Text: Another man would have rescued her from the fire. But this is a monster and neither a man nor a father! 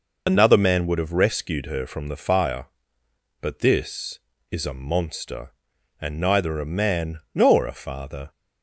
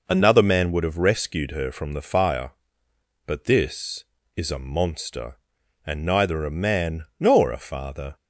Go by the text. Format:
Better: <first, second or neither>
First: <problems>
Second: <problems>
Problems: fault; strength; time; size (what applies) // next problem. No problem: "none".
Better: second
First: loses the start of "Another"; at 0.2 s; 45 ms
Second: none